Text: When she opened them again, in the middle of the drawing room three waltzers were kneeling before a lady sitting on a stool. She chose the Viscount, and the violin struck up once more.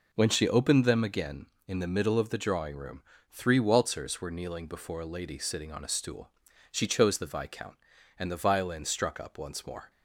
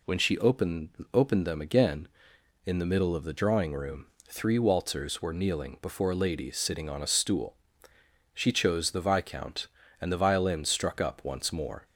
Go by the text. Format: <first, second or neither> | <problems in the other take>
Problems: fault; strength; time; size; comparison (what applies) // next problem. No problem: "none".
first | says "opened" twice; at 1.1 s // pauses between "room" and "three"; slight; at 4.0 s; 0.22 s long; slight in the first